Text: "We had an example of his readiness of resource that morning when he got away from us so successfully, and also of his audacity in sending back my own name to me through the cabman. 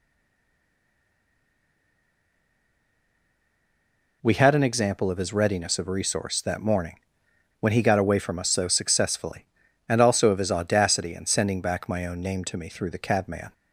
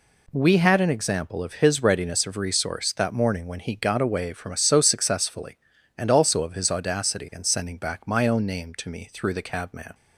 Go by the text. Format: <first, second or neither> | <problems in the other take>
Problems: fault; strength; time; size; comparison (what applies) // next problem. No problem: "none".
second | stays silent before the first word; strong; until 4.2 s; 4.2 s long // pauses between "morning" and "when"; noticeable; at 6.9 s; 0.60 s long